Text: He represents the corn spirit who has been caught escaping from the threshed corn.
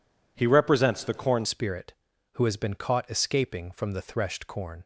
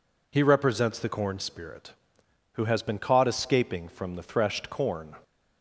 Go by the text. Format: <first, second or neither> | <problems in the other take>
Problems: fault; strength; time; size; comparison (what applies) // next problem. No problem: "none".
second | changes voice at "spirit"; from 1.4 s on; 3.4 s long